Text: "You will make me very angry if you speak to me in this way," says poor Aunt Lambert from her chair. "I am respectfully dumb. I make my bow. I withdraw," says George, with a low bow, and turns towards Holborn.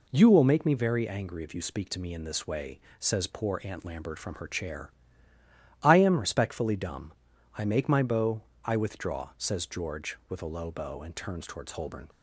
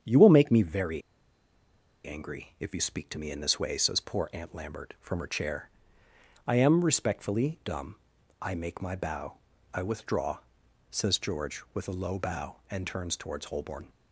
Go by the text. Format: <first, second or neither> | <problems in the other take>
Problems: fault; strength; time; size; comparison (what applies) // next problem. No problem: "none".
first | starts louder than the rest; strong; until 2.0 s; 8 dB // pauses between "very" and "angry"; at 1.0 s; 1.0 s long